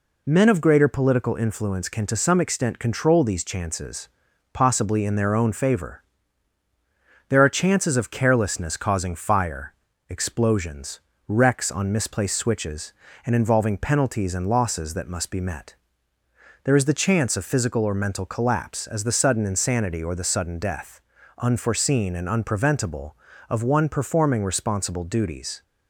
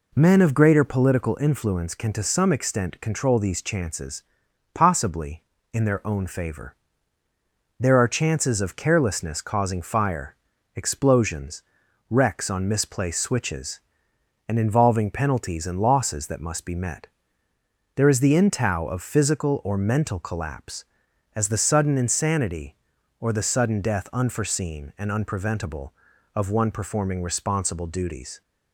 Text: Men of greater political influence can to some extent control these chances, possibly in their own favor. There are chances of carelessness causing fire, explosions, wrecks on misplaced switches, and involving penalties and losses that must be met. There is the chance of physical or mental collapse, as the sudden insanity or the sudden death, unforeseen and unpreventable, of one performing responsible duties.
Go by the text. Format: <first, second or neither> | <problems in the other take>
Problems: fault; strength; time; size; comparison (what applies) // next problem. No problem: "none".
first | says "intow" for "chance"; at 18.3 s